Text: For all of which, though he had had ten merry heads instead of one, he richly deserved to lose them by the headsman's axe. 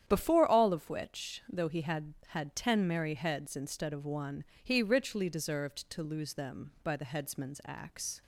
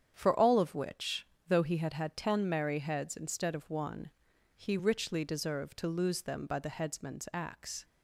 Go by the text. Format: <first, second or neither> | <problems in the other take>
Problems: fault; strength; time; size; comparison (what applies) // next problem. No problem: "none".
second | starts louder than the rest; strong; until 1.0 s; 9.5 dB; strong in the second // says "Before" for "For"; at 0.0 s